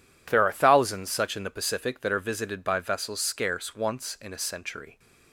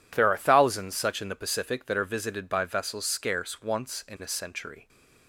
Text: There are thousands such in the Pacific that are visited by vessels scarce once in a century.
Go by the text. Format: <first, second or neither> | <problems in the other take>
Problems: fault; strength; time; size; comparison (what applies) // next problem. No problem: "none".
neither | none